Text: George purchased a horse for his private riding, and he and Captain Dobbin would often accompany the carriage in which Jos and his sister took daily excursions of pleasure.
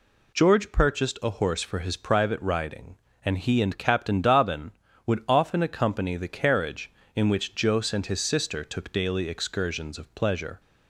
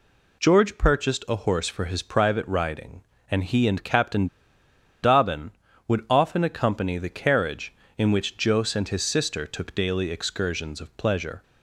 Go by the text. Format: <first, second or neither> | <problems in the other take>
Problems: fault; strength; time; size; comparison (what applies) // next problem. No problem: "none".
first | pauses between "Captain" and "Dobbin"; noticeable; at 4.2 s; 0.76 s long